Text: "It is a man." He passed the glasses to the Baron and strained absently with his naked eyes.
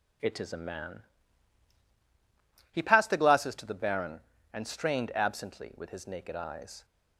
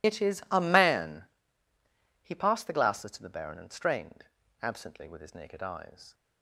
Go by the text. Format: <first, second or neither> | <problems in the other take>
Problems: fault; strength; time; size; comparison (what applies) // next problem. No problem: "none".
first | loses the start of "It"; at 0.0 s; 45 ms // pauses between "strained" and "absently"; slight; at 4.2 s; 0.36 s long